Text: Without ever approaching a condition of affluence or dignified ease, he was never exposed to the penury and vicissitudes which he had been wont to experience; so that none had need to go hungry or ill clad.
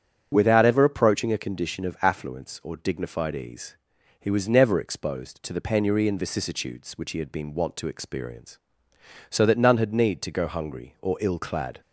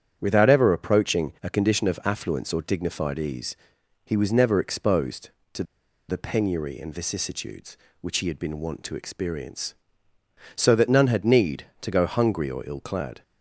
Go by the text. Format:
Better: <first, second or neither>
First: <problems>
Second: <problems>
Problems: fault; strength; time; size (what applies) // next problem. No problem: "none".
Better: first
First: starts louder than the rest; strong; until 1.3 s; 8 dB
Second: starts louder than the rest; strong; until 1.2 s; 9 dB // pauses between "to" and "the"; at 5.6 s; 0.45 s long